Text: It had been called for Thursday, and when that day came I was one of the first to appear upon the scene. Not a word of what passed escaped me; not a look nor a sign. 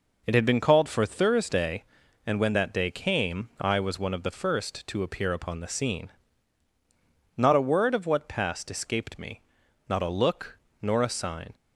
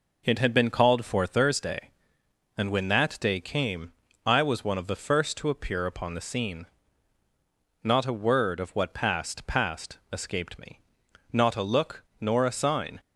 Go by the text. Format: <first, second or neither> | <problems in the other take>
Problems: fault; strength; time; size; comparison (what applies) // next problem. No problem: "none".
first | pauses between "came" and "I"; slight; at 3.9 s; 0.32 s long // says "passed" twice; at 9.4 s // pauses between "look" and "nor"; slight; at 12.0 s; 0.15 s long; slight in the first